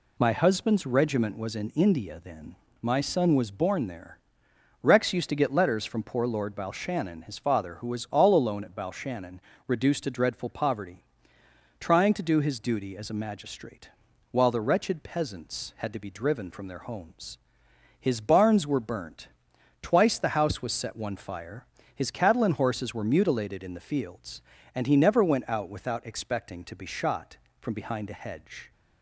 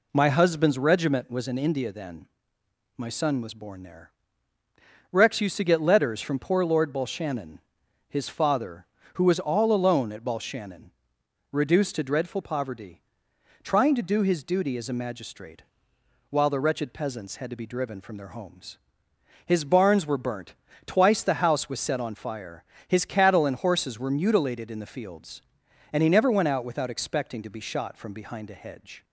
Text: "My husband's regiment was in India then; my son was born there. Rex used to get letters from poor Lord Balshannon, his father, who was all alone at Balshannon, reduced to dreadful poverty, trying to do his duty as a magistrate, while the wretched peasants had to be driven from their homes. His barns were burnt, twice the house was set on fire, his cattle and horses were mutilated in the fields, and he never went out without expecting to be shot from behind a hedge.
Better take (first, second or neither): second